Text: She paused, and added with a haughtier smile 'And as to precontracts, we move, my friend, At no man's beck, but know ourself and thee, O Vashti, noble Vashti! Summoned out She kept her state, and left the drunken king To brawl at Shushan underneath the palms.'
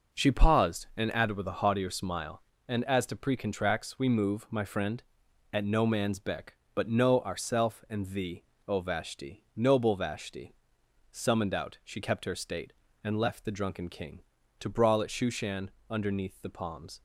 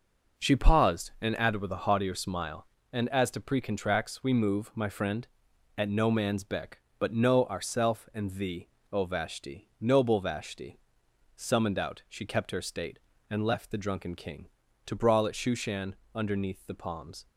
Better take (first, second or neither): neither